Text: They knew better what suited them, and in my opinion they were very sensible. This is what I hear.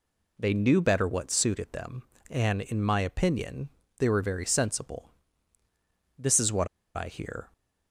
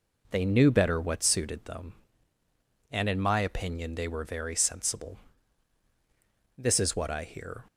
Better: second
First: pauses between "opinion" and "they"; slight; at 3.6 s; 0.30 s long // pauses between "what" and "I"; slight; at 6.6 s; 0.28 s long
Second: none

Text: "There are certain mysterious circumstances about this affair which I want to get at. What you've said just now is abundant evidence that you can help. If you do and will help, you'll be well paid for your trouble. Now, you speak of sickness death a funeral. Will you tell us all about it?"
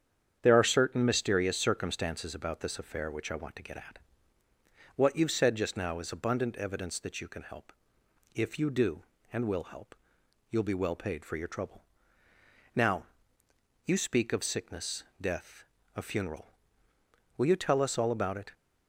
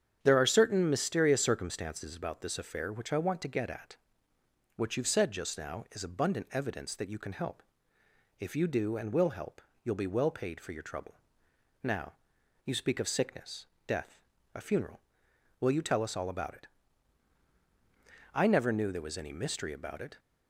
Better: first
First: starts louder than the rest; strong; until 1.4 s; 8.5 dB // pauses between "sickness" and "death"; slight; at 15.0 s; 0.16 s long // pauses between "death" and "a"; slight; at 15.6 s; 0.30 s long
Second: starts louder than the rest; strong; until 1.2 s; 8.5 dB // pauses between "sickness" and "death"; slight; at 13.6 s; 0.20 s long // pauses between "death" and "a"; slight; at 14.2 s; 0.34 s long // goes on to say "I never knew there was any mystery about it"; strong; from 18.3 s on; 1.8 s long

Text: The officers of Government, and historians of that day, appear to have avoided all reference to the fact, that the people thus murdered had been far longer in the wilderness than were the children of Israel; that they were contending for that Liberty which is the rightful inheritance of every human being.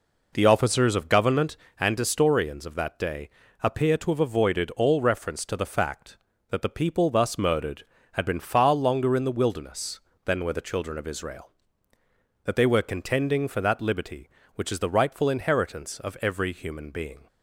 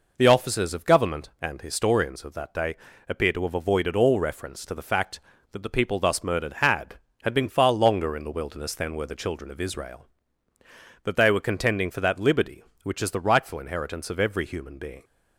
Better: first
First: none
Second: says "had" twice; at 7.2 s

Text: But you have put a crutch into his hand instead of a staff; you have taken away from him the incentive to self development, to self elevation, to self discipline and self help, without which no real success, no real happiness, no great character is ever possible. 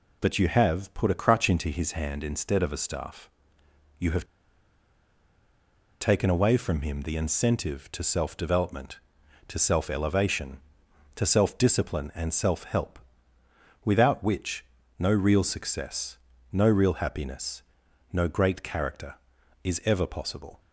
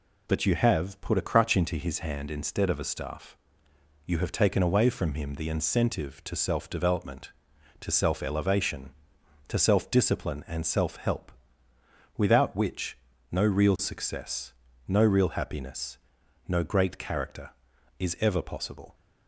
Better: second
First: pauses between "have" and "taken"; strong; at 4.2 s; 1.7 s long // pauses between "which" and "no"; slight; at 14.6 s; 0.34 s long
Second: pauses between "which" and "no"; slight; at 12.9 s; 0.34 s long

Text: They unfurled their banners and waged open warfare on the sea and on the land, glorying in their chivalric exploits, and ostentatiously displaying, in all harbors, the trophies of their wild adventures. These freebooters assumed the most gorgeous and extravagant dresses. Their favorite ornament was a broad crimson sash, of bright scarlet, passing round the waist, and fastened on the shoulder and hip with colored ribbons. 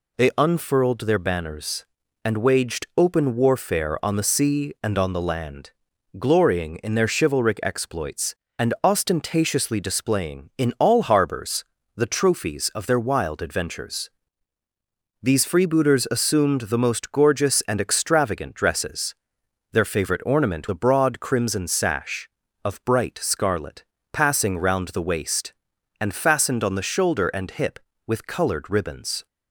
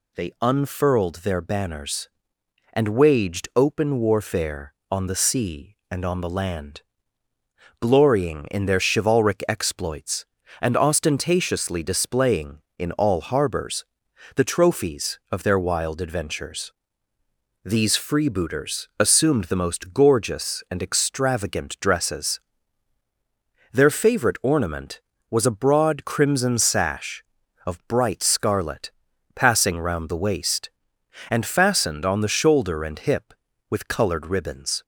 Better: second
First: skips "was"; at 20.6 s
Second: none

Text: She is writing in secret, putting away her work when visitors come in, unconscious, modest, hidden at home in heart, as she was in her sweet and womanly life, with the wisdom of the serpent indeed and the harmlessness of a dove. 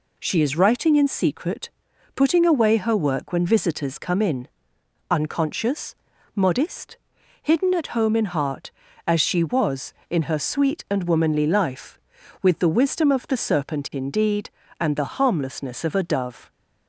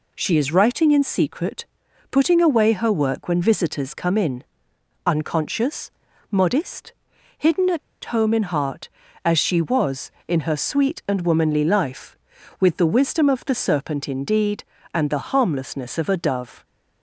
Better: first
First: none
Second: pauses between "at" and "home"; slight; at 7.7 s; 0.25 s long

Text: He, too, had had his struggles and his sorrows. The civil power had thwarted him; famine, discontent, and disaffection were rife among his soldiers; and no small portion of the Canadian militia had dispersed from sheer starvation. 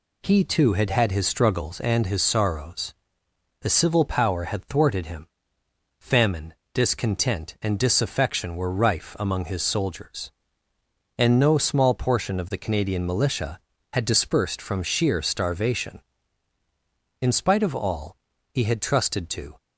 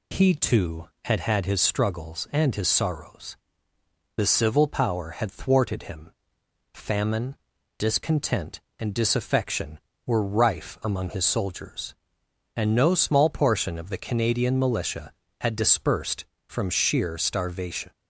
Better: second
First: goes on to say "In spite of all he had trusted to"; strong; from 17.2 s on; 2.3 s long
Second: none

